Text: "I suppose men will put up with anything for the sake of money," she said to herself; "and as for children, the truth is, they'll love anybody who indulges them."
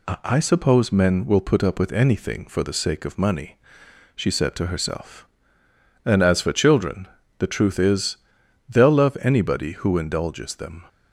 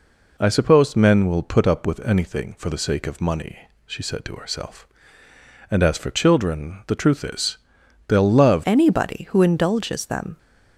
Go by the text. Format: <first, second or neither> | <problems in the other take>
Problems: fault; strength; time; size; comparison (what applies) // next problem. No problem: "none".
first | changes voice at "anybody"; from 8.6 s on; 1.7 s long